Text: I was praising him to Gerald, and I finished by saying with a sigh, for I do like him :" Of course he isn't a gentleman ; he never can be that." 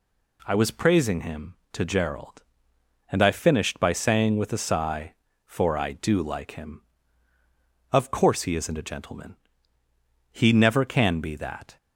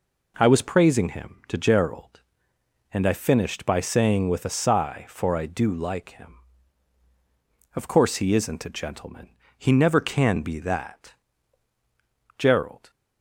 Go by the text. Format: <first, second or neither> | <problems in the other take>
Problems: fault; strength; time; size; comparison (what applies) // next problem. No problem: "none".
first | goes on to say "Gerald"; from 12.3 s on; 0.54 s long